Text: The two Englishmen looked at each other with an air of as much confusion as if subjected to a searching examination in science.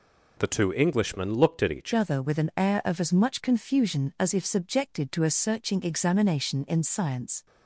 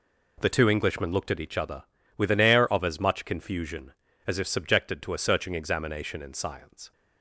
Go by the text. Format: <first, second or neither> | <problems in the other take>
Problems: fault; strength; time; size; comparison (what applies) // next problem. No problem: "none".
second | changes voice at "other"; from 1.9 s on; 5.5 s long